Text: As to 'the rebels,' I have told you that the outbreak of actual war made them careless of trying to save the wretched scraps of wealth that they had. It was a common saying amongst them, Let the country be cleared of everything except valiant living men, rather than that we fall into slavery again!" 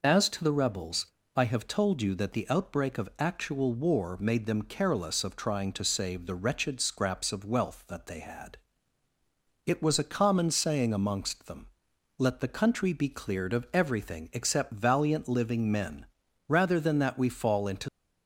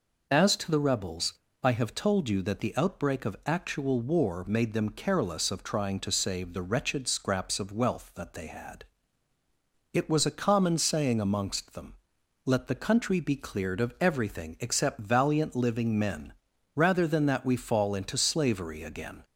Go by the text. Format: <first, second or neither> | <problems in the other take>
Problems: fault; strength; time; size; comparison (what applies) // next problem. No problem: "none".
second | stops before "slavery again"; at 17.8 s